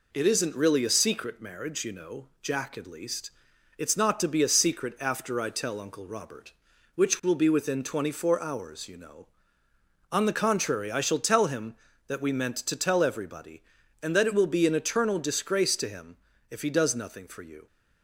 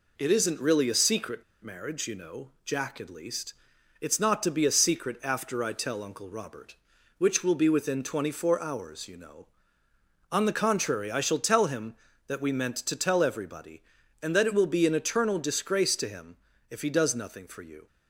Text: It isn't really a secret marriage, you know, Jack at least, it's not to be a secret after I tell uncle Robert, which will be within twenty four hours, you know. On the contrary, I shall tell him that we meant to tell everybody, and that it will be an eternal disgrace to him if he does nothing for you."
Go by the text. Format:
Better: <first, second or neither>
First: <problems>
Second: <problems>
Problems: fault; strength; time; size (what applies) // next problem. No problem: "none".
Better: first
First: pauses between "him" and "if"; slight; at 16.1 s; 0.32 s long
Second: pauses between "secret" and "marriage"; slight; at 1.4 s; 0.20 s long // pauses between "him" and "if"; slight; at 16.3 s; 0.32 s long